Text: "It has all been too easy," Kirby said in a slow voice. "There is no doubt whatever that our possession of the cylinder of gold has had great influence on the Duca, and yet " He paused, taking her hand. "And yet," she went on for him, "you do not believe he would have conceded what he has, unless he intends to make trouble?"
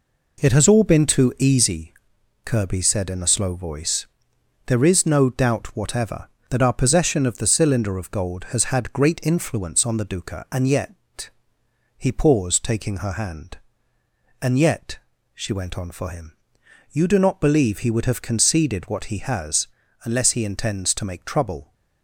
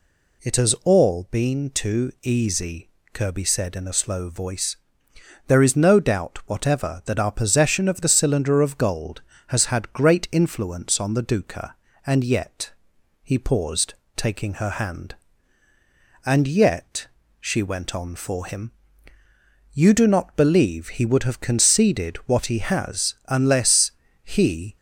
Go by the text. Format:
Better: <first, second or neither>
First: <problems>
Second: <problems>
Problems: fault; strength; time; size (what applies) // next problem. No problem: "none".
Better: first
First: none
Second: pauses between "unless" and "he"; slight; at 23.8 s; 0.34 s long // stops before "intends to make trouble"; at 24.7 s